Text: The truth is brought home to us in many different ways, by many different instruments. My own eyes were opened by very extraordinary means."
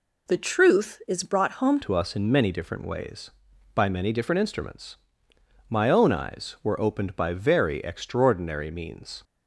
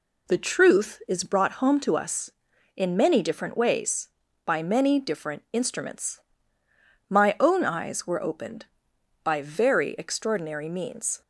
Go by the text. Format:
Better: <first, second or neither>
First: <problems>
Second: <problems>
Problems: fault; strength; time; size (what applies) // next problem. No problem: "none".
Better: second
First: changes voice at "to"; from 1.8 s on; 7.4 s long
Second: none